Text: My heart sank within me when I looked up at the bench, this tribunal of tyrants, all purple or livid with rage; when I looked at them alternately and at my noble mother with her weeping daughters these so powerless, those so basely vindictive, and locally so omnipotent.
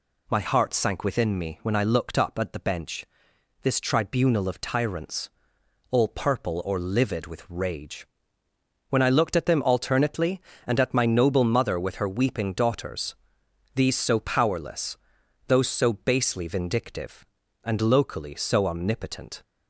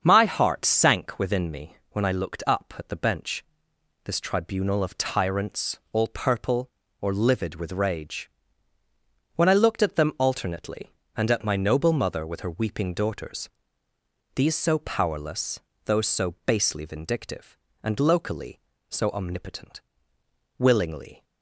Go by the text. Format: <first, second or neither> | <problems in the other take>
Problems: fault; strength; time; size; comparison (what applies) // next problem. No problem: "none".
first | starts louder than the rest; until 1.0 s; 7 dB // pauses between "me" and "when"; slight; at 1.7 s; 0.16 s long // pauses between "daughters" and "these"; noticeable; at 13.4 s; 0.86 s long; noticeable in the first // goes on to say "Willingly"; noticeable; from 20.5 s on; 0.64 s long